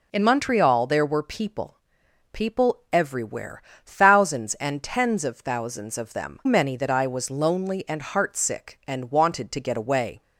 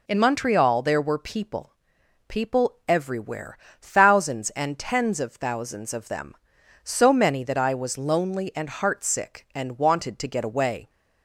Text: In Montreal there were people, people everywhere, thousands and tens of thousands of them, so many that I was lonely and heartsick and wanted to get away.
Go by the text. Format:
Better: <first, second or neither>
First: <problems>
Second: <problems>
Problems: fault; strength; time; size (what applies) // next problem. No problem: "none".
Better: second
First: skips "so"; at 6.4 s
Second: none